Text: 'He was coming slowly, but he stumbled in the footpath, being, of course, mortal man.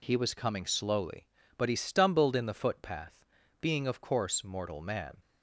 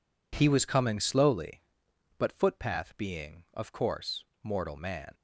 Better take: first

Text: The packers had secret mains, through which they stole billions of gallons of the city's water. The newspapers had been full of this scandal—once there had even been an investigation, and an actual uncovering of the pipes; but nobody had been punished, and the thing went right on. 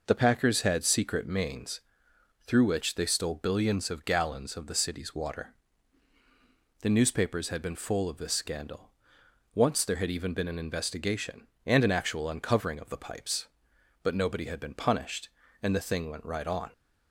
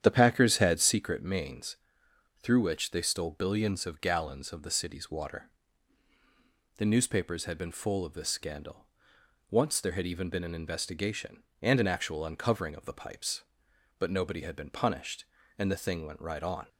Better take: first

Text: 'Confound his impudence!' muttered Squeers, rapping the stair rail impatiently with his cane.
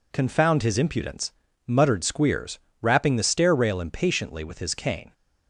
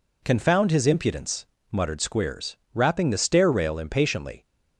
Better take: first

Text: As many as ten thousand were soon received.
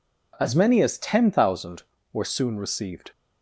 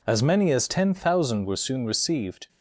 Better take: neither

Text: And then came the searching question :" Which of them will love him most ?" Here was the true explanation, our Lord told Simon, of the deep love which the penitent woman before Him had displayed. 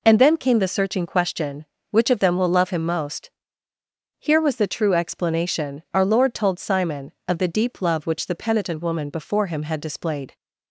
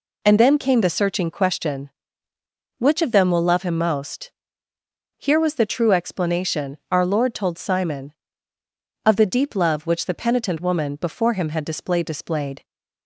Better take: first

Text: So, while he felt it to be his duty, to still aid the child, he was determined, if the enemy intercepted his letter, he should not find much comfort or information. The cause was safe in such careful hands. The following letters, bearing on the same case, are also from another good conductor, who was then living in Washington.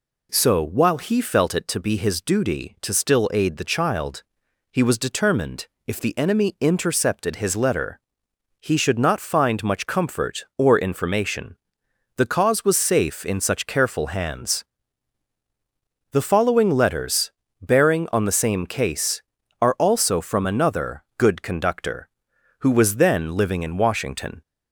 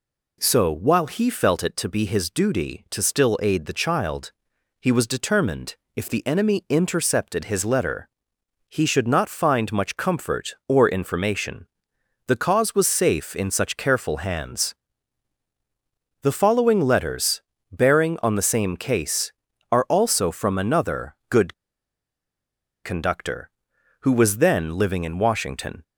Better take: first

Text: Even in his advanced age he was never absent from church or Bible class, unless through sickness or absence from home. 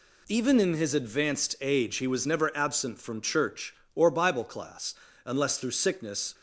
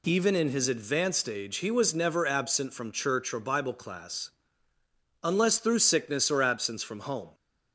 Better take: second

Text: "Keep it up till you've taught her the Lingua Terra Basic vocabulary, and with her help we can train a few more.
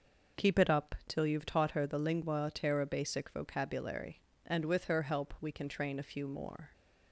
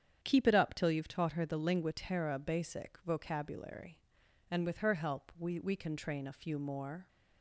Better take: first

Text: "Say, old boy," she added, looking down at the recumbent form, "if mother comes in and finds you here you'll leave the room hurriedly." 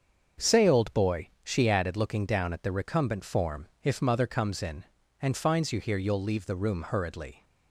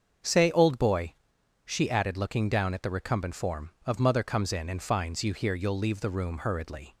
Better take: first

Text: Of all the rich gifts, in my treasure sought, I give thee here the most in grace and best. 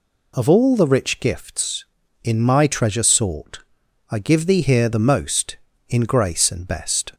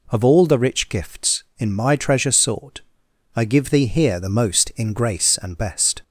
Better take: neither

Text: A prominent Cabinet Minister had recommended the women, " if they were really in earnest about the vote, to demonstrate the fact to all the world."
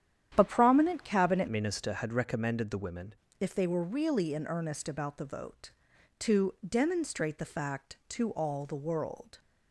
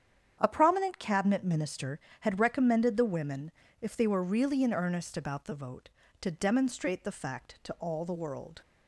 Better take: second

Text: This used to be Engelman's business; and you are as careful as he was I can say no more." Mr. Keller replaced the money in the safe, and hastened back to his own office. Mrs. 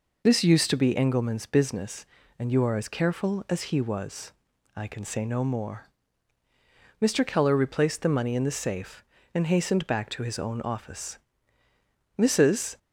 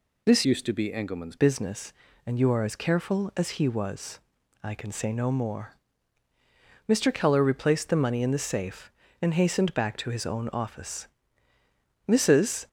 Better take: first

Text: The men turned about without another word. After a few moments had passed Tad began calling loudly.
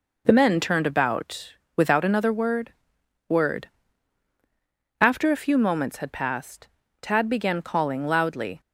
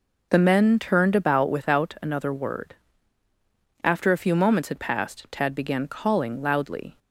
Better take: second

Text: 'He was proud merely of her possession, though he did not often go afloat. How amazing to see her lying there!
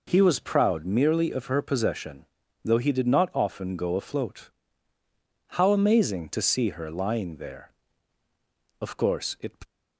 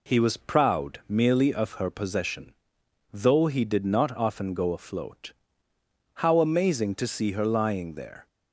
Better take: second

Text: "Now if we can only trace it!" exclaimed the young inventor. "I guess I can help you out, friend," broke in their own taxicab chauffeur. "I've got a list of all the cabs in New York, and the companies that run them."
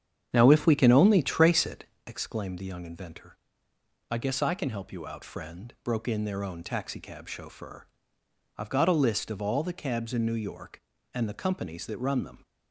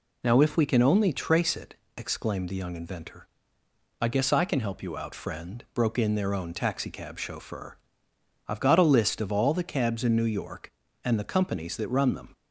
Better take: second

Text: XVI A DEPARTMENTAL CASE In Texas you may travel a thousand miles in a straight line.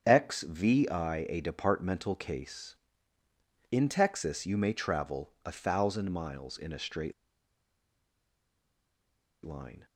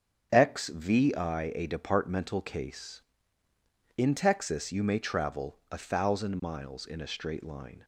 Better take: second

